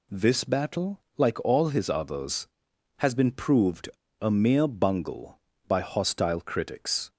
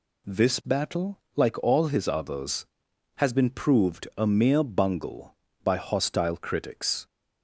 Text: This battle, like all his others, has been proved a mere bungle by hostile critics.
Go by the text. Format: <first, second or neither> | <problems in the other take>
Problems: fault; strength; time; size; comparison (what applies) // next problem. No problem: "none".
second | pauses between "proved" and "a"; slight; at 3.8 s; 0.32 s long